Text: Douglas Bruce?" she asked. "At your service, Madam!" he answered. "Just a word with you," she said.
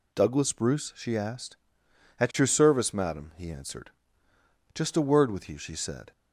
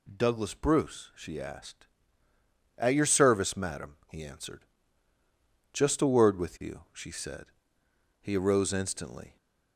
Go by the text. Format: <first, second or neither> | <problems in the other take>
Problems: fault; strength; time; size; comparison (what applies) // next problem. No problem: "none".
first | goes on to say "He arose instantly"; noticeable; from 8.2 s on; 1.1 s long